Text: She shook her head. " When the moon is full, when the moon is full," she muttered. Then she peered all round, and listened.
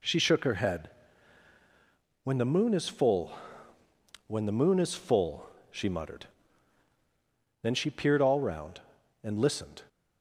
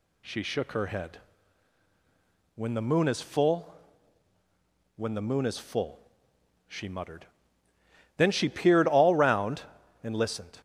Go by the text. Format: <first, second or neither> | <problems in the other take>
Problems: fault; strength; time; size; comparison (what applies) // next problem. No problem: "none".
neither | none